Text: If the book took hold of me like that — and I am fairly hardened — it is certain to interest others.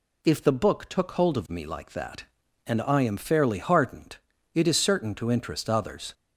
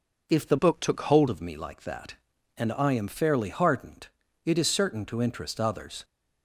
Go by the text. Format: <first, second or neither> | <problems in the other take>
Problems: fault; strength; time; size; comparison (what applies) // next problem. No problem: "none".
first | changes voice from "book" to "hold"; from 0.5 to 1.2 s; 0.7 s long